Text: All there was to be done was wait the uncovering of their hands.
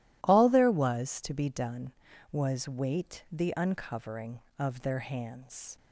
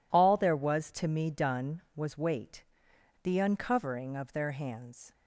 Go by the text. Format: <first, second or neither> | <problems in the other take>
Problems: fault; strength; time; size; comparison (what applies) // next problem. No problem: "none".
first | says "me" for "be"; at 1.0 s // pauses between "wait" and "the"; noticeable; at 2.6 s; 0.57 s long